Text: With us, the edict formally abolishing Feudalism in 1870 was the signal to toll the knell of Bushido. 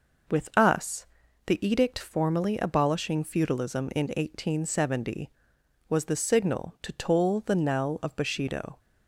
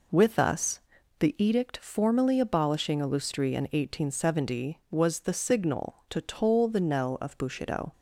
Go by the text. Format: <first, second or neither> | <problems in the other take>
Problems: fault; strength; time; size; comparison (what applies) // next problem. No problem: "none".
first | says "Illustri" for "Feudalism"; at 3.0 s